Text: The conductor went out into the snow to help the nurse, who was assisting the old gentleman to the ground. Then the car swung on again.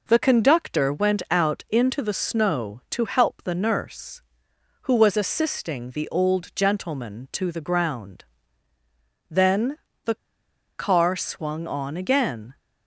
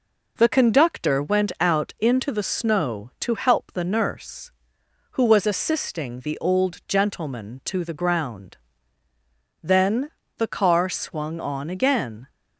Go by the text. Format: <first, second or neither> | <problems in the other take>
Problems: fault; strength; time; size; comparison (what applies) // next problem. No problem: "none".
second | pauses between "Then" and "the"; slight; at 9.7 s; 0.28 s long; slight in the second // pauses between "the" and "car"; noticeable; at 10.1 s; 0.62 s long